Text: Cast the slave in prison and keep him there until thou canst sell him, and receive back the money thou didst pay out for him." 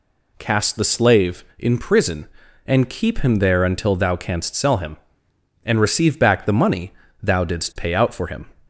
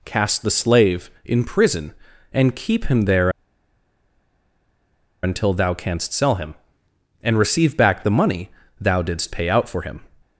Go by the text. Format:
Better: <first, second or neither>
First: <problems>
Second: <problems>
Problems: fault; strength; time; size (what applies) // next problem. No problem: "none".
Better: first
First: pauses between "money" and "thou"; slight; at 6.9 s; 0.30 s long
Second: pauses between "there" and "until"; strong; at 3.2 s; 1.9 s long // pauses between "money" and "thou"; slight; at 8.4 s; 0.30 s long